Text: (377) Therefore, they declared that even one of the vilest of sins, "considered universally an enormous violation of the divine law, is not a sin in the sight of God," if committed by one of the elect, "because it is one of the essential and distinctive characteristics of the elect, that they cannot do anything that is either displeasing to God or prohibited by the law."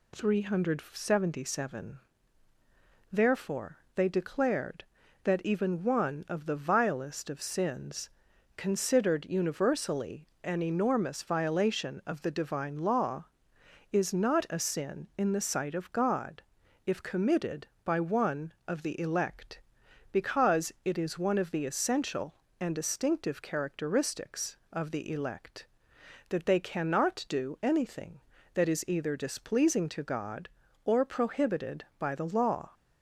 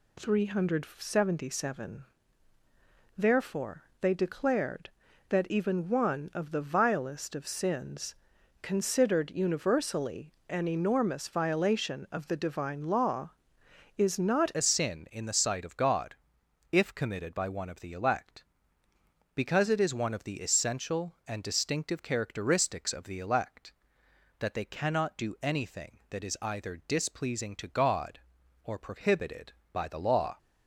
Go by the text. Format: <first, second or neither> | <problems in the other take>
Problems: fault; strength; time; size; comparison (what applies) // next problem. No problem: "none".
first | pauses between "universally" and "an"; slight; at 10.3 s; 0.16 s long; slight in the first // changes voice at "a"; from 14.5 s on; 15.8 s long